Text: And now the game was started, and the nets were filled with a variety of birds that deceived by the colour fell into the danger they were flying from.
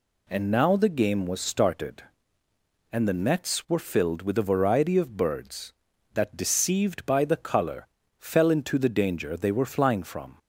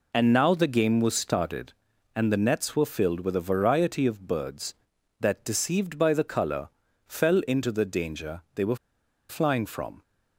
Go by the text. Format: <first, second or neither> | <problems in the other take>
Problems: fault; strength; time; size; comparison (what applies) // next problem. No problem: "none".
first | pauses between "colour" and "fell"; at 6.6 s; 0.38 s long; slight in the first // pauses between "were" and "flying"; noticeable; at 8.7 s; 0.53 s long